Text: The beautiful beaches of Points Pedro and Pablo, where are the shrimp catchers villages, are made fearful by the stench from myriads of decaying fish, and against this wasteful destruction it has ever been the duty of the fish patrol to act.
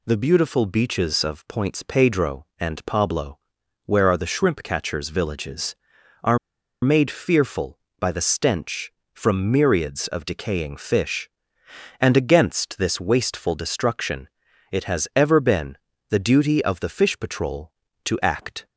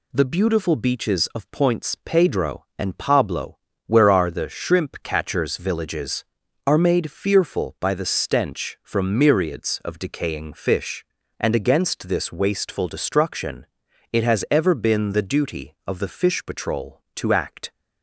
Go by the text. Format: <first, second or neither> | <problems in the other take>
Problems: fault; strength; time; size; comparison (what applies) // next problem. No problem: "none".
second | pauses between "are" and "made"; noticeable; at 6.3 s; 0.46 s long // pauses between "destruction" and "it"; at 14.2 s; 0.42 s long; also in the second // pauses between "been" and "the"; slight; at 15.7 s; 0.34 s long